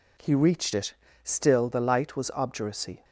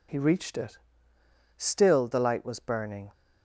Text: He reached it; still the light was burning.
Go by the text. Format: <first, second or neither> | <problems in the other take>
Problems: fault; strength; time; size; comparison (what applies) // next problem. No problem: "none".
second | says "obduracy" for "burning"; at 2.3 s